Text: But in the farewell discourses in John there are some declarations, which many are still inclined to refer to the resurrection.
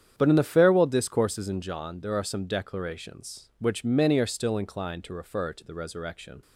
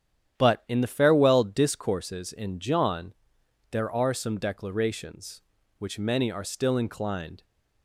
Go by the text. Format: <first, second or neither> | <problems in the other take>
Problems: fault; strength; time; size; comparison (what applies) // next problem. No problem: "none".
first | starts louder than the rest; strong; until 1.4 s; 10 dB; strong in the first // pauses between "John" and "there"; noticeable; at 3.1 s; 0.58 s long // stops before "to refer to the resurrection"; at 7.4 s